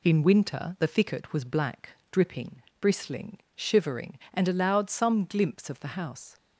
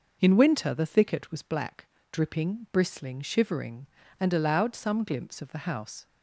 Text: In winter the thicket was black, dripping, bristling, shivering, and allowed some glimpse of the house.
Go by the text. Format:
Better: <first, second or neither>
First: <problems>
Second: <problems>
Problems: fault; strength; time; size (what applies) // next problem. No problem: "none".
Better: neither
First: none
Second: none